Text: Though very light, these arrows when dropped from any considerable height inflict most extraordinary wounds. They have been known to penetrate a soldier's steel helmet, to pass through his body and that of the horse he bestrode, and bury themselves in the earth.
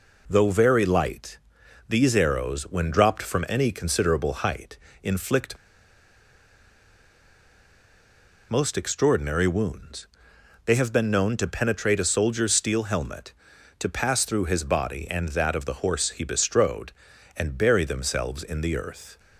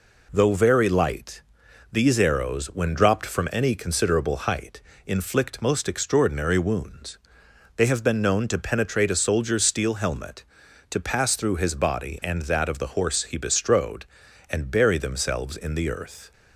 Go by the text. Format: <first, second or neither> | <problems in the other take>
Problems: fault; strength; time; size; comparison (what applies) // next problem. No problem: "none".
second | pauses between "height" and "inflict"; slight; at 4.7 s; 0.28 s long; slight in the second // pauses between "inflict" and "most"; strong; at 5.5 s; 2.9 s long